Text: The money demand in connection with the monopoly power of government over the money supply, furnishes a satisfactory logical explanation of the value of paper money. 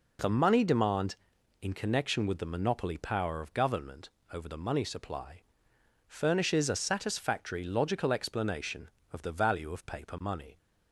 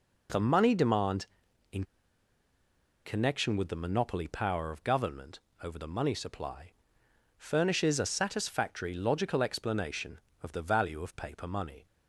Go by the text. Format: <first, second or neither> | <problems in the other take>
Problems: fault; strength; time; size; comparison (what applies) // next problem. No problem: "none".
first | pauses between "in" and "connection"; at 1.8 s; 1.2 s long // pauses between "government" and "over"; slight; at 5.4 s; 0.24 s long; slight in the first